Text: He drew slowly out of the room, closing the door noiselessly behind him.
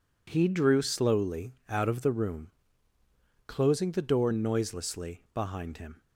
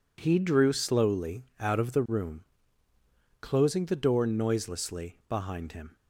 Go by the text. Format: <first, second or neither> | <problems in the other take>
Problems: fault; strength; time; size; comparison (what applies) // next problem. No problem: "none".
neither | pauses between "slowly" and "out"; slight; the same in both